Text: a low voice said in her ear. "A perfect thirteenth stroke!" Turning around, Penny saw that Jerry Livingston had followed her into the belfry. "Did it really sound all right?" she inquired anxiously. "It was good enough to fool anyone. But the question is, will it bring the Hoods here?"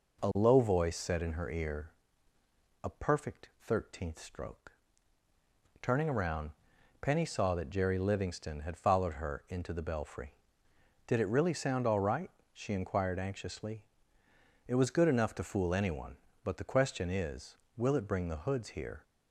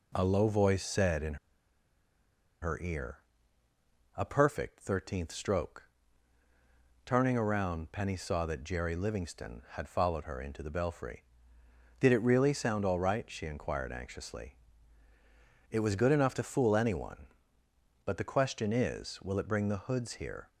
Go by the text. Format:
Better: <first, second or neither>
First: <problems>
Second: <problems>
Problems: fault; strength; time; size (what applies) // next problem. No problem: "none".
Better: first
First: none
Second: pauses between "in" and "her"; strong; at 1.3 s; 1.2 s long